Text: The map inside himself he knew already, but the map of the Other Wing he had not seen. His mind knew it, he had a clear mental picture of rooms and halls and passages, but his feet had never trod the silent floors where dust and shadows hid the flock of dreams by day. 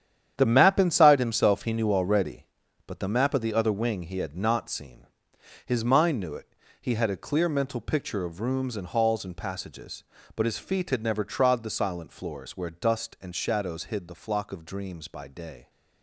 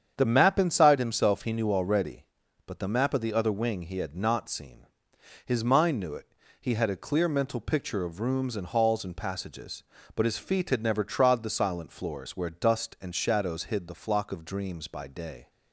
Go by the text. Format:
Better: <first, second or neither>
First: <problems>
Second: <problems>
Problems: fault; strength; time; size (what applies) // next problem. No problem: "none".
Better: second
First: gets quieter; strong; throughout; 11 dB // starts louder than the rest; strong; until 1.3 s; 9 dB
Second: starts louder than the rest; strong; until 1.1 s; 8 dB